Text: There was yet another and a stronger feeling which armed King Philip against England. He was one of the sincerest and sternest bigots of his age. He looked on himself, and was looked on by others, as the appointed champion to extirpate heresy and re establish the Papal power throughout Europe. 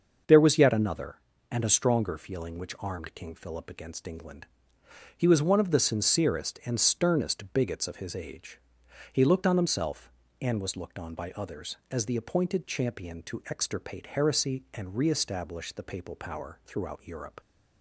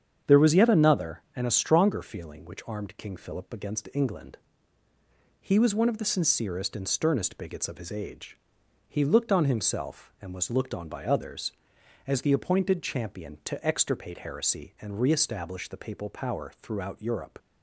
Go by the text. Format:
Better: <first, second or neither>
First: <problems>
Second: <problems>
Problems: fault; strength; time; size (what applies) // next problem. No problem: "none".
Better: neither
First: starts louder than the rest; until 1.6 s; 6.5 dB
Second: starts louder than the rest; strong; until 1.4 s; 8 dB